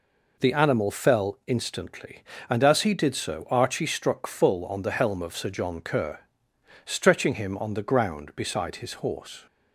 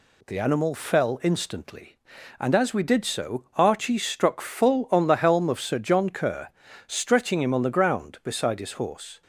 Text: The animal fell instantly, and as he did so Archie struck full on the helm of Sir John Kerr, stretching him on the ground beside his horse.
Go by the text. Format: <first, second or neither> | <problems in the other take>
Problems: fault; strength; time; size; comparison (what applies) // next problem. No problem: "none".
first | says "we" for "he"; at 2.7 s